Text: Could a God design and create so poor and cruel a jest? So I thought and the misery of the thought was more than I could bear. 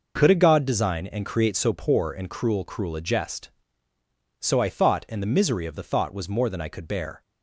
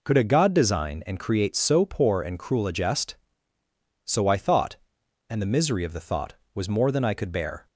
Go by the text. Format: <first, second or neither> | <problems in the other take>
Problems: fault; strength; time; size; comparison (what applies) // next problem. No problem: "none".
second | says "cruel" twice; at 2.6 s